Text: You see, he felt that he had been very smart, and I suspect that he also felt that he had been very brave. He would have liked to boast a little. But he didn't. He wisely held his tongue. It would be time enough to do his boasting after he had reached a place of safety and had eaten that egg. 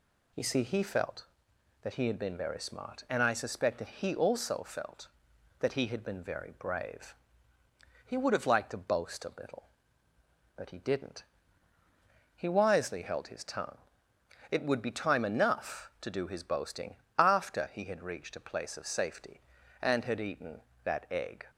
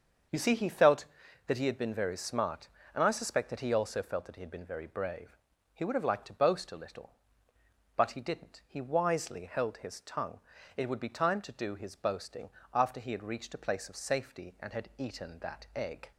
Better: first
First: pauses between "boasting" and "after"; slight; at 16.9 s; 0.22 s long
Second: starts louder than the rest; until 1.7 s; 6.5 dB // skips "enough"; at 11.4 s // pauses between "boasting" and "after"; slight; at 12.4 s; 0.24 s long

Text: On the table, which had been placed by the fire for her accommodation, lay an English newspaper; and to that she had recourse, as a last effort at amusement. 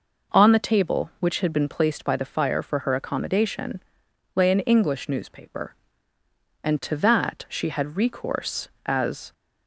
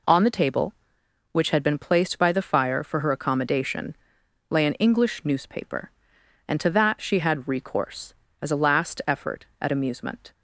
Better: second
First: stops before "a last effort at amusement"; at 9.3 s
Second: none

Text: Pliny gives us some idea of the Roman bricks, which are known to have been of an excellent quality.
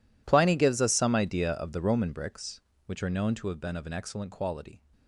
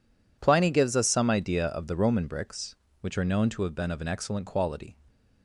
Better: second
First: gets quieter; strong; throughout; 19 dB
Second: none

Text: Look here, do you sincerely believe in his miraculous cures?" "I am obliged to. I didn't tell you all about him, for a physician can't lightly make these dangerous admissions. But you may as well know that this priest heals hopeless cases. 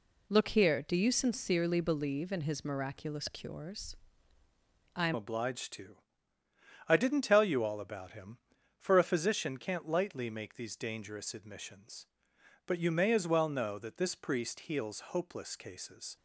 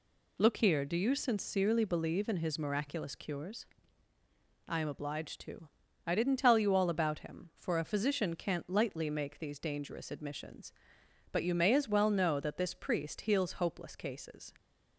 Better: second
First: changes voice at "obliged"; from 5.1 s on; 11.0 s long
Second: none

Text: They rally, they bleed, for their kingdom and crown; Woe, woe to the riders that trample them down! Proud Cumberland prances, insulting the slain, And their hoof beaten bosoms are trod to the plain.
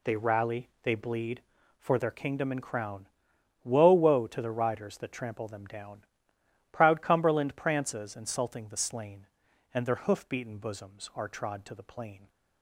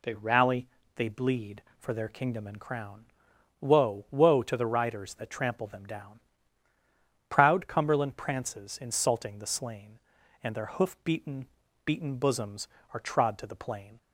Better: first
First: none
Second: says "beaten" twice; at 11.8 s

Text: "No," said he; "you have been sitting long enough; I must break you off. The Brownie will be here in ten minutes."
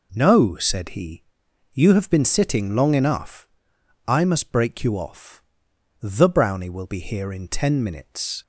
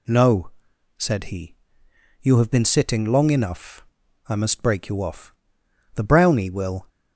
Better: first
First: none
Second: stops before "be here in ten minutes"; at 6.8 s

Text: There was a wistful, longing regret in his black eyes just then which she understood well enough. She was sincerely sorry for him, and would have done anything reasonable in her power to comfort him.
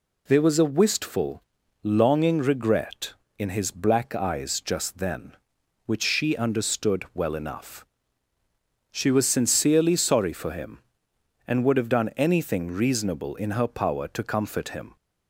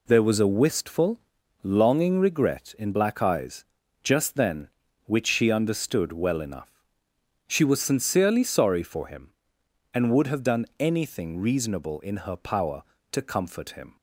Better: first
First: none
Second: skips "his"; at 2.9 s // pauses between "eyes" and "just"; at 3.6 s; 0.40 s long

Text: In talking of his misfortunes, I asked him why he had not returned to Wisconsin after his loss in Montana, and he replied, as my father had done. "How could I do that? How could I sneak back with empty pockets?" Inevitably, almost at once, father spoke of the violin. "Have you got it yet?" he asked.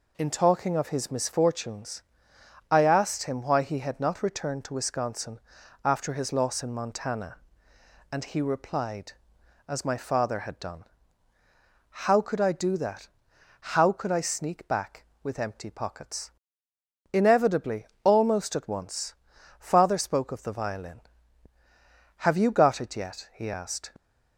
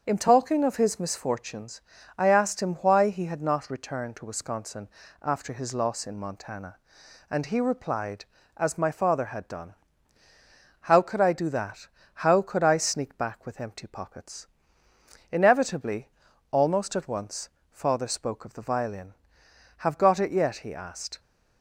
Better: first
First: pauses between "Wisconsin" and "after"; at 5.3 s; 0.44 s long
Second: starts louder than the rest; until 1.0 s; 7 dB // pauses between "Wisconsin" and "after"; slight; at 4.8 s; 0.34 s long // skips "you"; at 19.9 s

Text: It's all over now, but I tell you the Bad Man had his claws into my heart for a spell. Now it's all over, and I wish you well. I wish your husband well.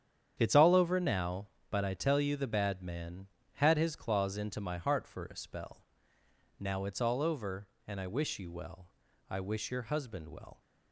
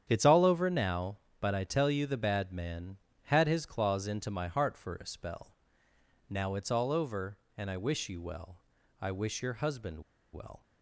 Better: first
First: starts louder than the rest; strong; until 1.3 s; 9 dB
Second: starts louder than the rest; strong; until 1.0 s; 9 dB // pauses between "husband" and "well"; slight; at 10.0 s; 0.33 s long

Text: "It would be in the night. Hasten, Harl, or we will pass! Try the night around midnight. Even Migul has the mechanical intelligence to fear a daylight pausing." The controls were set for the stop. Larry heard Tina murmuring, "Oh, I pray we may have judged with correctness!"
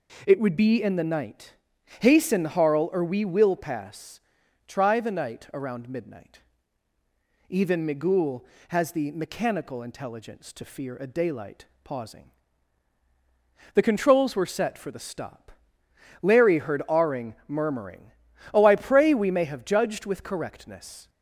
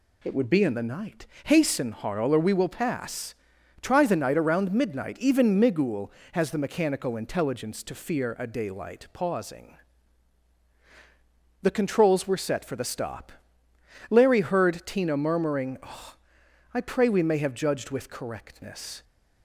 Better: second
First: pauses between "daylight" and "pausing"; slight; at 11.6 s; 0.18 s long // says "Aring" for "Tina"; at 16.8 s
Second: none

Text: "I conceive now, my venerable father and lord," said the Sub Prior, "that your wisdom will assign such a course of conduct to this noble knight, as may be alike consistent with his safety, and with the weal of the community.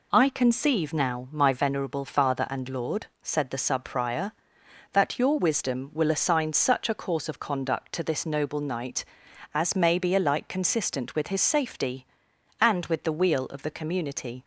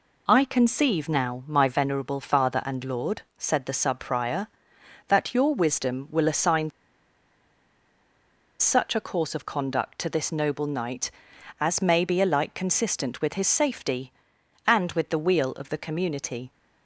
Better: first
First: none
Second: pauses between "assign" and "such"; strong; at 6.6 s; 1.8 s long

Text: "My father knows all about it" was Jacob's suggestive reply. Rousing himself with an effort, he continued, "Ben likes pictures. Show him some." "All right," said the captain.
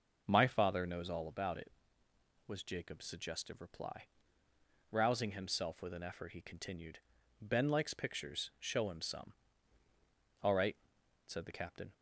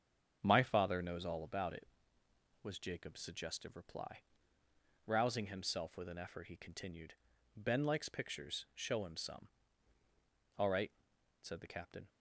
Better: first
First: none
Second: gets quieter; strong; throughout; 7 dB

